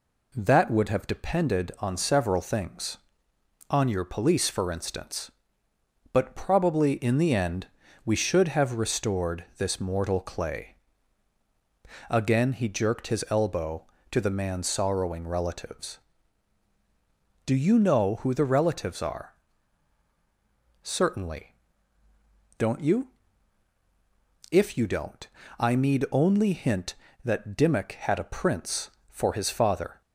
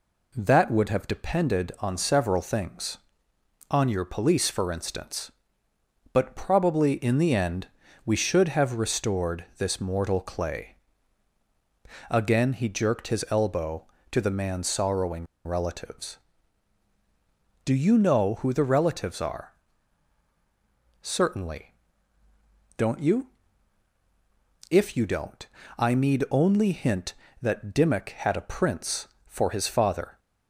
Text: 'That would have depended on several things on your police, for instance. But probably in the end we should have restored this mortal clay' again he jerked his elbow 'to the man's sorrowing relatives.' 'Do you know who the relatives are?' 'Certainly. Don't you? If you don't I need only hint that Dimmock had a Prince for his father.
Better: first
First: pauses between "end" and "we"; at 7.6 s; 0.38 s long // pauses between "clay" and "again"; strong; at 10.7 s; 1.3 s long // pauses between "don't" and "I"; slight; at 25.2 s; 0.32 s long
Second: pauses between "end" and "we"; at 7.6 s; 0.38 s long // pauses between "clay" and "again"; strong; at 10.7 s; 1.3 s long // pauses between "sorrowing" and "relatives"; slight; at 15.2 s; 0.20 s long // pauses between "don't" and "I"; slight; at 25.4 s; 0.32 s long

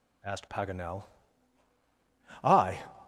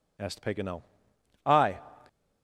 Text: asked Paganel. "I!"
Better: neither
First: none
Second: none

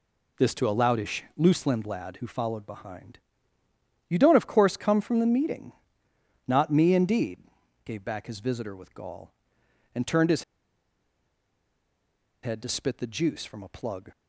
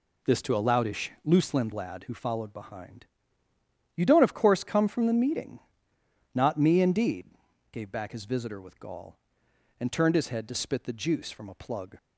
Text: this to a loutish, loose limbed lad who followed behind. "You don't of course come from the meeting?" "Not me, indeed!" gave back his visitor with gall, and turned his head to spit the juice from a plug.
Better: second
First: pauses between "his" and "head"; strong; at 10.4 s; 2.0 s long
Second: none

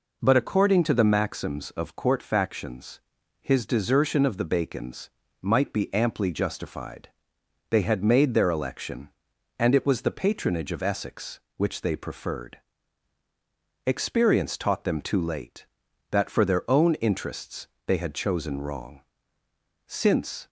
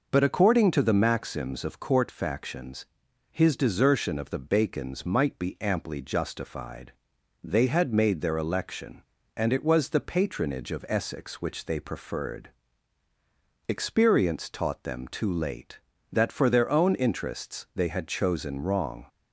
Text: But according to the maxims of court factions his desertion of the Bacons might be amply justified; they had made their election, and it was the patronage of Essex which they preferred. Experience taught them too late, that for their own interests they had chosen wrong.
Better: second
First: pauses between "factions" and "his"; at 3.0 s; 0.40 s long // pauses between "Bacons" and "might"; slight; at 5.0 s; 0.32 s long // pauses between "interests" and "they"; slight; at 17.6 s; 0.20 s long // goes on to say "Since"; noticeable; from 19.8 s on; 0.62 s long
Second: pauses between "factions" and "his"; at 2.8 s; 0.44 s long

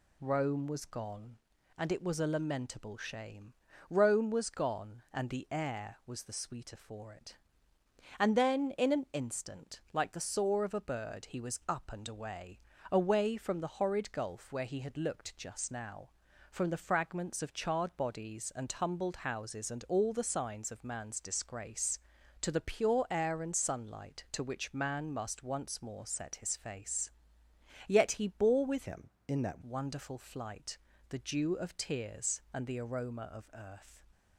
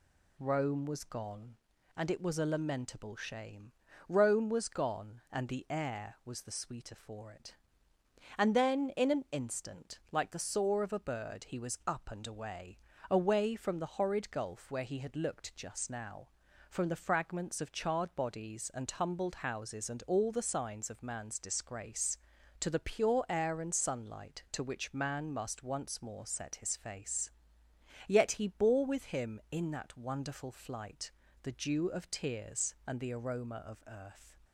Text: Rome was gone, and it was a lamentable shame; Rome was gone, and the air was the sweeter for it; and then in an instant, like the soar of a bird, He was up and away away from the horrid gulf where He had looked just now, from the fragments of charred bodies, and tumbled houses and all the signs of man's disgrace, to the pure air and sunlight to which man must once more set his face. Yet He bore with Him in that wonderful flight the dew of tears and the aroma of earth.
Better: second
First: pauses between "away" and "away"; slight; at 12.5 s; 0.32 s long // changes voice from "Him" to "that"; from 28.9 to 29.6 s; 0.7 s long // pauses between "flight" and "the"; slight; at 30.7 s; 0.32 s long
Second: pauses between "away" and "away"; slight; at 12.7 s; 0.32 s long // pauses between "flight" and "the"; slight; at 31.1 s; 0.32 s long

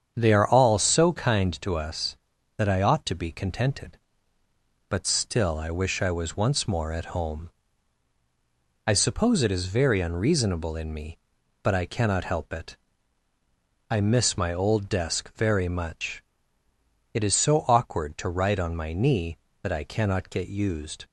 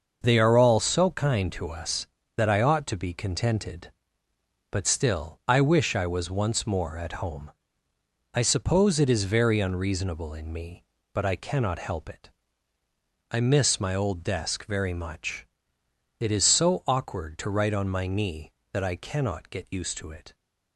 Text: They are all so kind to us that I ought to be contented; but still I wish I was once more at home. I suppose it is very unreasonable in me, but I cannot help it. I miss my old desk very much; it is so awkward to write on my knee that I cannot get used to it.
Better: second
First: starts louder than the rest; strong; until 1.1 s; 7.5 dB // stops before "to it"; at 21.0 s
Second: starts louder than the rest; until 1.2 s; 6 dB

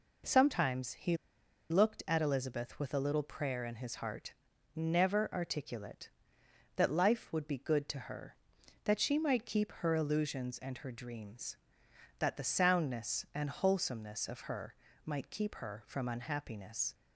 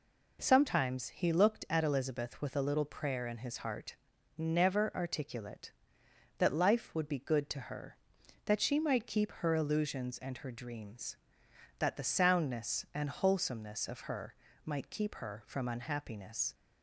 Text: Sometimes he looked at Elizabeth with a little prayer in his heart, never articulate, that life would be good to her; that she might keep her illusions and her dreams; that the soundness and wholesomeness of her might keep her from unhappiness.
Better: second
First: pauses between "he" and "looked"; noticeable; at 1.1 s; 0.55 s long // pauses between "her" and "might"; slight; at 14.7 s; 0.28 s long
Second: pauses between "her" and "might"; slight; at 14.3 s; 0.28 s long

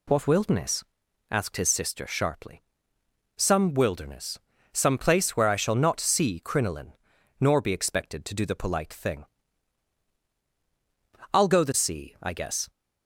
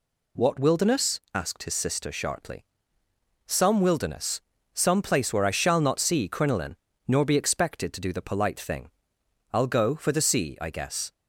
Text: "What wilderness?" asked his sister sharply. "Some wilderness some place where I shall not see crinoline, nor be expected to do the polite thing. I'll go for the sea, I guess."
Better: second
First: pauses between "wilderness" and "some"; slight; at 4.3 s; 0.34 s long // skips "for"; at 11.6 s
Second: pauses between "wilderness" and "some"; slight; at 4.4 s; 0.32 s long

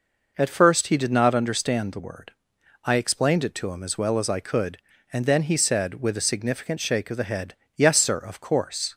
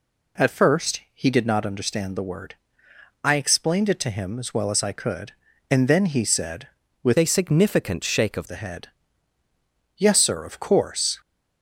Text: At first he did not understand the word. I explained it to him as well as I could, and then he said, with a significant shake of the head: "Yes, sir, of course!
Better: first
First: none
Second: changes voice from "a" to "of"; from 7.1 to 8.4 s; 1.3 s long

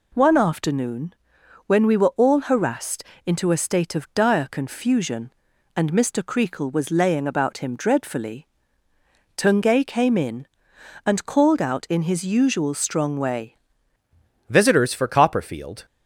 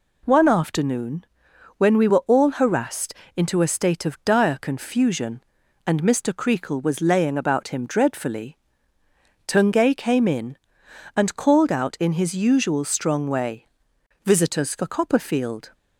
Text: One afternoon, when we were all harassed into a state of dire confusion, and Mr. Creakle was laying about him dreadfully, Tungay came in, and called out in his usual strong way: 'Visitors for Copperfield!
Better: second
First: pauses between "harassed" and "into"; slight; at 3.0 s; 0.22 s long // changes voice at "Visitors"; from 14.4 s on; 1.4 s long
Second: pauses between "harassed" and "into"; slight; at 3.1 s; 0.22 s long

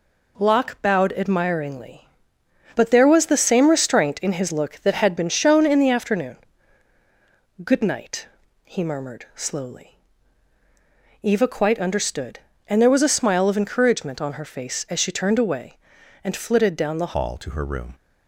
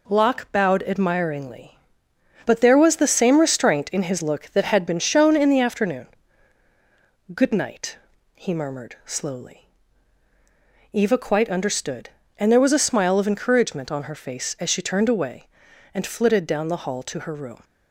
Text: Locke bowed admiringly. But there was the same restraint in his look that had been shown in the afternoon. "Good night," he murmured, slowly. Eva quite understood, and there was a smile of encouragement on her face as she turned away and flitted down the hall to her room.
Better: second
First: changes voice at "hall"; from 17.1 s on; 0.8 s long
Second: none

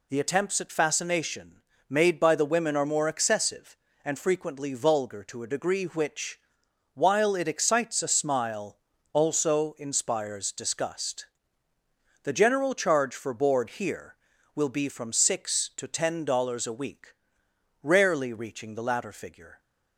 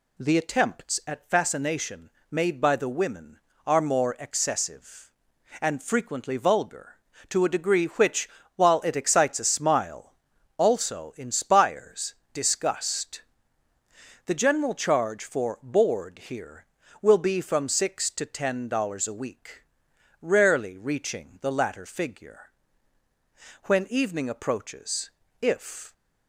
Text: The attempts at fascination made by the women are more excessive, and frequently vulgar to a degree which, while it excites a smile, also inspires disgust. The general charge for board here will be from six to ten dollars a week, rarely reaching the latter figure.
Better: first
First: pauses between "fascination" and "made"; slight; at 1.6 s; 0.28 s long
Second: pauses between "fascination" and "made"; slight; at 2.0 s; 0.22 s long // pauses between "inspires" and "disgust"; slight; at 12.1 s; 0.18 s long // goes on to say "When evening approaches if"; strong; from 23.6 s on; 2.2 s long

